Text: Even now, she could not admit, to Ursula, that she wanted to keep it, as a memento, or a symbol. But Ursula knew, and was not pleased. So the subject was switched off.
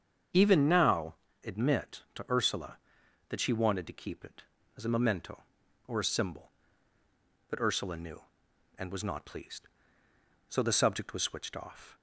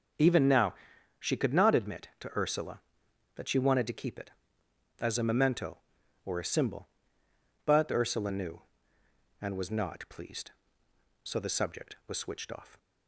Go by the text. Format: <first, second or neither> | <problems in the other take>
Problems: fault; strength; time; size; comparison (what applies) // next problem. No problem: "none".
second | starts louder than the rest; strong; until 1.6 s; 7 dB; also in the second // skips "she could not"; at 1.2 s